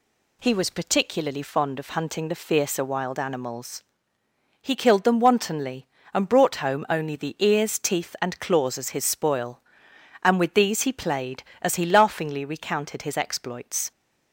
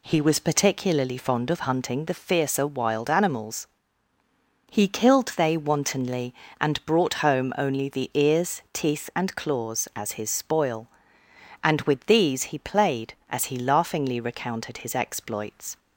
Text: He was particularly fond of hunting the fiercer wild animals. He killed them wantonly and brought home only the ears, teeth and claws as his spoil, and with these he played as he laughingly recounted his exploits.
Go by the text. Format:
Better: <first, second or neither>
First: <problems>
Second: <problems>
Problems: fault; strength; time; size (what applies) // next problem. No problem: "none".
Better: first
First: none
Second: says "they" for "them"; at 5.3 s